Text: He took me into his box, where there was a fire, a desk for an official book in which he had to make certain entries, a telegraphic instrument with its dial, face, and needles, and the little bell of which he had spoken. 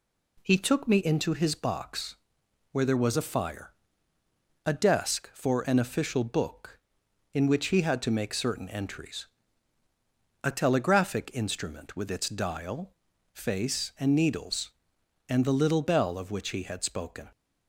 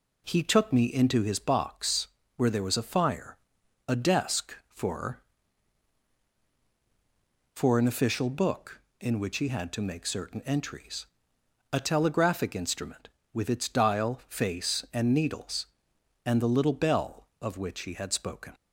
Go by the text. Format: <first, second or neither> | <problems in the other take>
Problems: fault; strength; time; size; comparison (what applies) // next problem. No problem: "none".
first | says "for" twice; at 7.5 s